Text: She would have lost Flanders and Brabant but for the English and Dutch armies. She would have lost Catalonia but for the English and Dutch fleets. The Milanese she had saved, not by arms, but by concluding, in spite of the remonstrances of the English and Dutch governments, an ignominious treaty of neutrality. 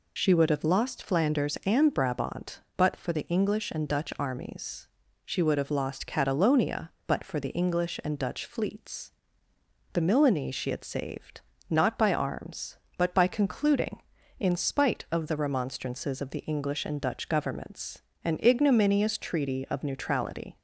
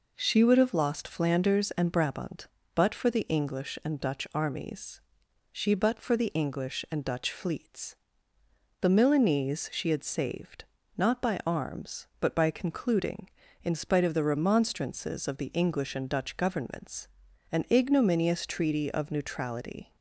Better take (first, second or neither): first